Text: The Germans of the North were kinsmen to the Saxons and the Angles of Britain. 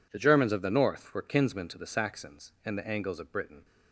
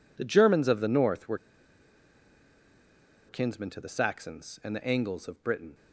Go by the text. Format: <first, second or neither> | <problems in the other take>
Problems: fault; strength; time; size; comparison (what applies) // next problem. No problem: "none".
first | pauses between "were" and "kinsmen"; strong; at 1.3 s; 1.9 s long